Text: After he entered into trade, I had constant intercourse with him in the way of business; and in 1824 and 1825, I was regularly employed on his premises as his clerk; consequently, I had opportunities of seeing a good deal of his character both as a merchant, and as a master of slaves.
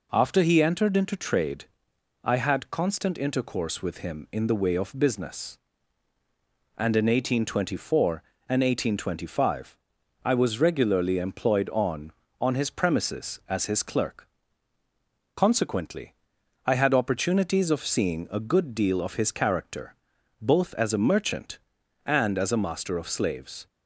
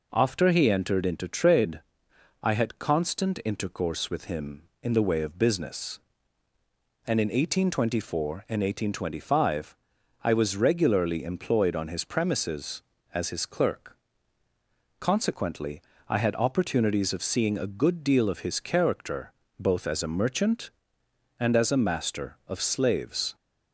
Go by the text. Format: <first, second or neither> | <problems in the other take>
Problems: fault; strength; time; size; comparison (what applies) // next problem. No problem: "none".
second | says "on" twice; at 12.4 s // pauses between "character" and "both"; at 19.9 s; 0.44 s long; slight in the second